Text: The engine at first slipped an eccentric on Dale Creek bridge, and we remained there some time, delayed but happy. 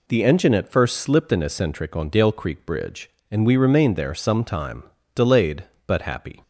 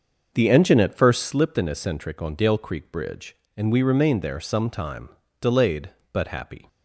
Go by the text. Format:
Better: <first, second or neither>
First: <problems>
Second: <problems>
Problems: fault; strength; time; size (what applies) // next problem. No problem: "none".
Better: first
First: none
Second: starts louder than the rest; until 1.4 s; 6 dB